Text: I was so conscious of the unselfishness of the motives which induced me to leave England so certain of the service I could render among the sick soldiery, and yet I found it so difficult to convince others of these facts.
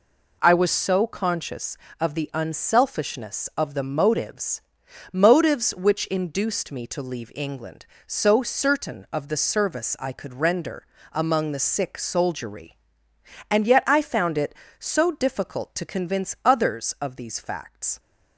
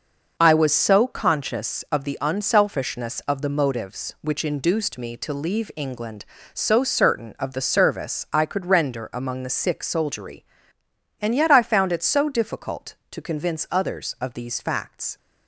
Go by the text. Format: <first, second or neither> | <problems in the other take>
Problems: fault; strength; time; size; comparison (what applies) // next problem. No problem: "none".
second | says "motives" twice; at 5.1 s // pauses between "render" and "among"; slight; at 10.8 s; 0.26 s long